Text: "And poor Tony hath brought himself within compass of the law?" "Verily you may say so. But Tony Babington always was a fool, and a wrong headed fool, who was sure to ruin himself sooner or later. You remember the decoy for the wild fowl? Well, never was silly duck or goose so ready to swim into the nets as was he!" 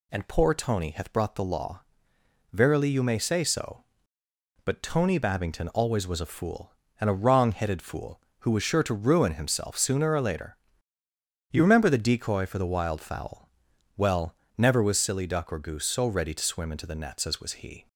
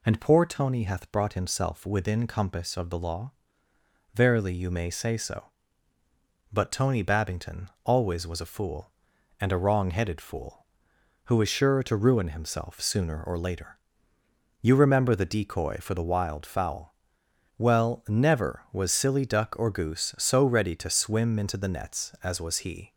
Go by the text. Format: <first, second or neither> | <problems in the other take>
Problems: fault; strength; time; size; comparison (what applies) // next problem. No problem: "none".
second | skips "himself within compass of"; at 1.3 s